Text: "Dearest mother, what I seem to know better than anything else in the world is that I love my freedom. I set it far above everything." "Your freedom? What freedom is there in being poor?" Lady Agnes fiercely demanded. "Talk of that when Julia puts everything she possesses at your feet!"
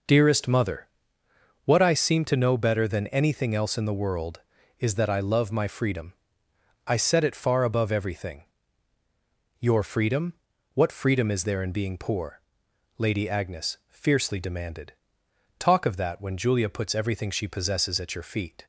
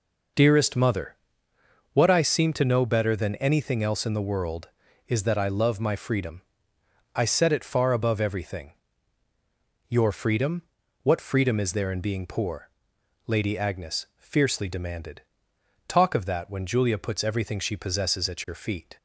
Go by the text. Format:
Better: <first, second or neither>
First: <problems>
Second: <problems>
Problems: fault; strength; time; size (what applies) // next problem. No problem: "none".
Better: neither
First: none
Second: none